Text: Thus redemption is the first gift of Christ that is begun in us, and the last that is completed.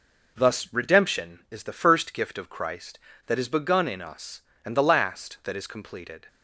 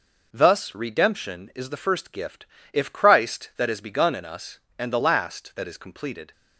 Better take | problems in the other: first | says "if" for "of"; at 2.7 s

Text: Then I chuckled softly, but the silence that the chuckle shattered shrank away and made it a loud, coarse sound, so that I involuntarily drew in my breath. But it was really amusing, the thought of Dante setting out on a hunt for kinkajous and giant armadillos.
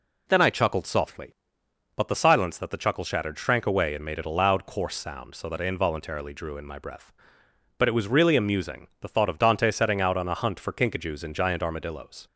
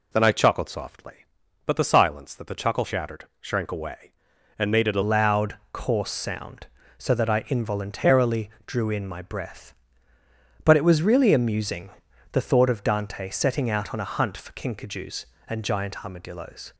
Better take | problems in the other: first | pauses between "shattered" and "shrank"; slight; at 3.2 s; 0.16 s long // changes voice at "loud"; from 5.0 s on; 11.7 s long // pauses between "involuntarily" and "drew"; slight; at 8.4 s; 0.16 s long

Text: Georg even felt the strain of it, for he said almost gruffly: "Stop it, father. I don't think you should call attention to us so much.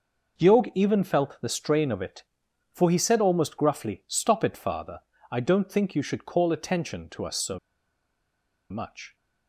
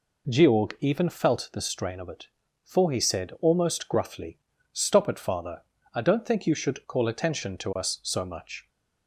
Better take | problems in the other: second | pauses between "so" and "much"; at 7.5 s; 1.1 s long

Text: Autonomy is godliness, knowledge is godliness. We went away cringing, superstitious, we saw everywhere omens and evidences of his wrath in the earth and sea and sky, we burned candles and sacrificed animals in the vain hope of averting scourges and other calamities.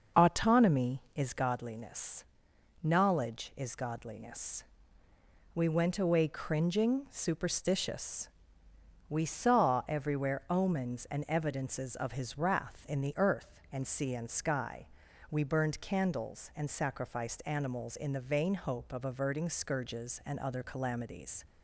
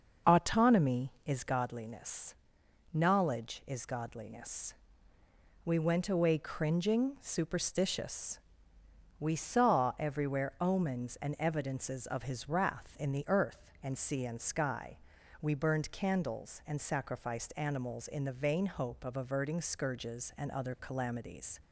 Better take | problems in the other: neither | none

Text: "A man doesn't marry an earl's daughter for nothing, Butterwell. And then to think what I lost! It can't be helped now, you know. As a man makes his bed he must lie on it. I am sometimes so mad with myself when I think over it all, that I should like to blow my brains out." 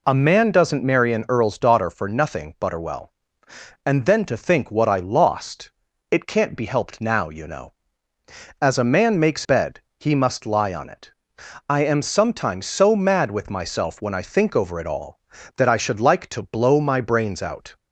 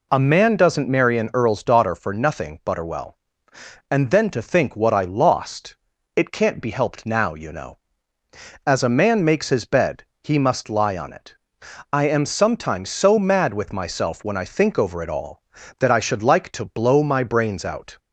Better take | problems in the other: second | skips "his"; at 9.4 s // pauses between "bed" and "he"; slight; at 9.8 s; 0.18 s long; slight in the second

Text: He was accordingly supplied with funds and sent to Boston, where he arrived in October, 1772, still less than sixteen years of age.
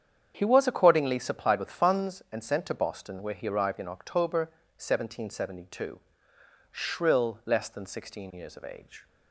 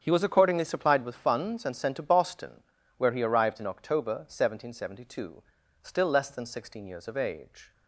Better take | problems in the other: second | starts louder than the rest; strong; until 1.3 s; 8 dB; strong in the second // says "shrill" for "still"; at 6.7 s

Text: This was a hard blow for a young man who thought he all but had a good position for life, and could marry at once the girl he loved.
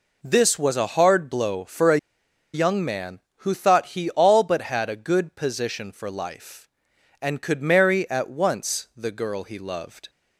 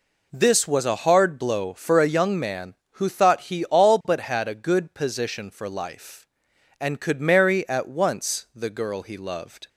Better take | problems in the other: second | pauses between "a" and "young"; noticeable; at 1.9 s; 0.56 s long

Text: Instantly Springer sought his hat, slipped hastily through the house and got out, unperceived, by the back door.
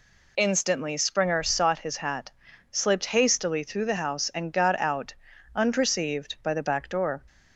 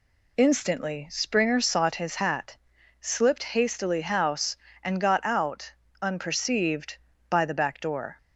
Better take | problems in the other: first | skips "through the"; at 4.0 s

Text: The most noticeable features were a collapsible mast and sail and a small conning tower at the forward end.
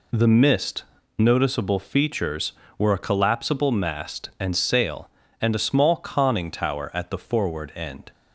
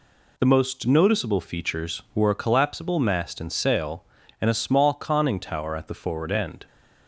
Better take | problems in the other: second | says "mist" for "most"; at 0.2 s

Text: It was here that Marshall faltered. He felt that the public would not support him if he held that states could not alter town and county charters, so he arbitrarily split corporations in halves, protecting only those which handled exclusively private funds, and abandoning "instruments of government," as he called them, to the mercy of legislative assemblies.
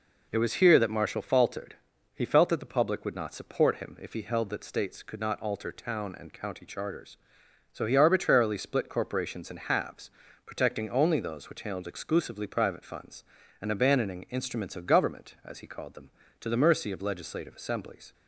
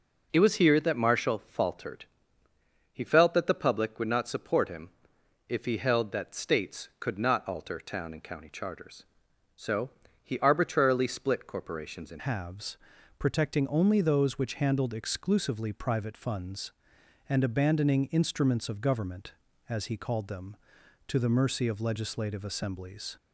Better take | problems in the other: first | pauses between "him" and "if"; noticeable; at 4.8 s; 0.58 s long // pauses between "so" and "he"; slight; at 9.8 s; 0.32 s long // changes voice at "halves"; from 12.1 s on; 11.0 s long

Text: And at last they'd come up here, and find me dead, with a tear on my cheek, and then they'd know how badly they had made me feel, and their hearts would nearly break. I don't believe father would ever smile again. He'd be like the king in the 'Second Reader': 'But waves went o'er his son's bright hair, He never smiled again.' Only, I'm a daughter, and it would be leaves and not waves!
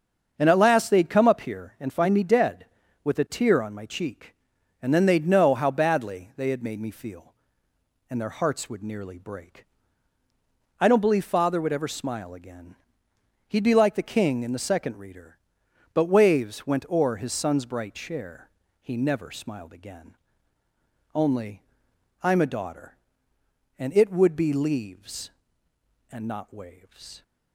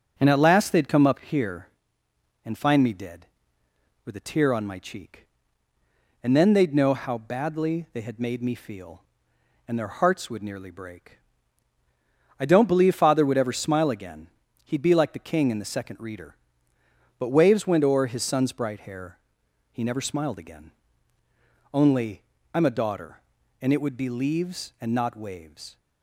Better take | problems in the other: second | starts louder than the rest; until 1.3 s; 7 dB; also in the second // says "chair" for "hair"; at 17.9 s

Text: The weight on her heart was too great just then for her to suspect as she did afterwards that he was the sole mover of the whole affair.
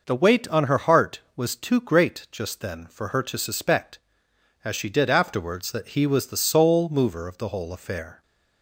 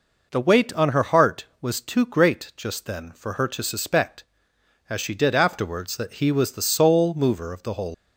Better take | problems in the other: first | stops before "affair"; at 7.9 s

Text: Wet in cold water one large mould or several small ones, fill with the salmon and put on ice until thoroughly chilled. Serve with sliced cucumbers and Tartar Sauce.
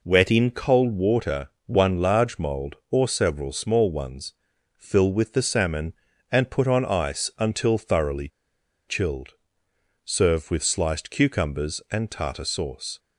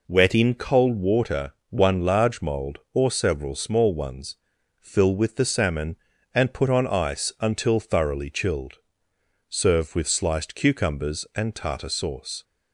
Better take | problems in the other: second | pauses between "water" and "one"; slight; at 1.4 s; 0.18 s long; slight in the second // pauses between "thoroughly" and "chilled"; noticeable; at 8.2 s; 0.60 s long

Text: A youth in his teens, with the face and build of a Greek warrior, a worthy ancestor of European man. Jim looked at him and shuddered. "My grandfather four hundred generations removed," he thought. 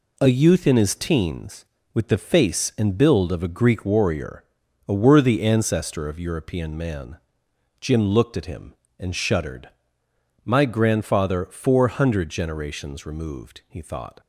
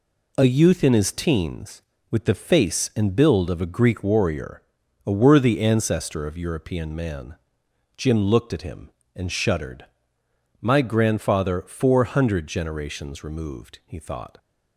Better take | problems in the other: neither | none

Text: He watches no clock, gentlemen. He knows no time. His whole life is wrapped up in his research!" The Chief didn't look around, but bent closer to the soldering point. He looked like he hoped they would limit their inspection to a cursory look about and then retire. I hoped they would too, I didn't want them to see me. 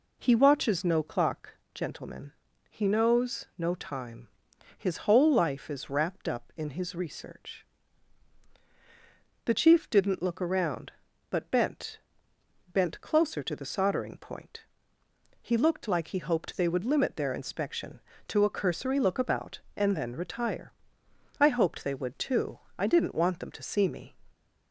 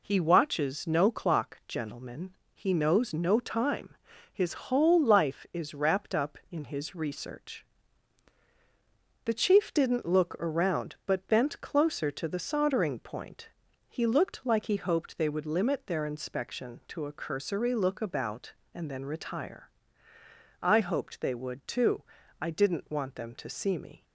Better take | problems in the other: second | says "bent" twice; at 12.7 s

